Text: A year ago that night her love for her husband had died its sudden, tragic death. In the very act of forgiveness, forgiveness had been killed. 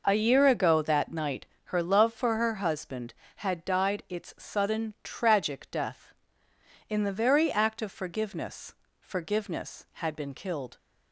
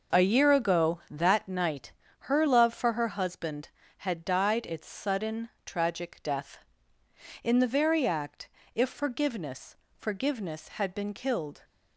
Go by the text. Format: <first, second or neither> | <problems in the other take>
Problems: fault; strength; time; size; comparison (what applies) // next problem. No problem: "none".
first | pauses between "night" and "her"; slight; at 1.9 s; 0.34 s long; slight in the first // says "if" for "of"; at 8.7 s